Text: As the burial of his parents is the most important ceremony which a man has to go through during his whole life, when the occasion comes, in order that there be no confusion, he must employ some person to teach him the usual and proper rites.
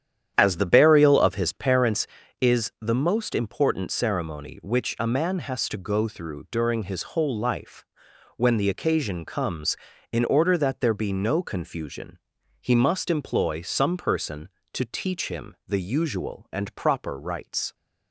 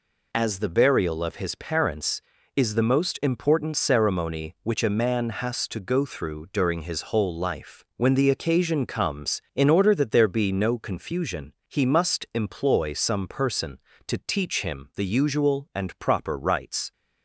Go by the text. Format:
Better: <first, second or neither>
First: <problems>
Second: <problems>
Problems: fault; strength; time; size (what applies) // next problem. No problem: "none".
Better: second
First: starts louder than the rest; strong; until 1.9 s; 9.5 dB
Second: none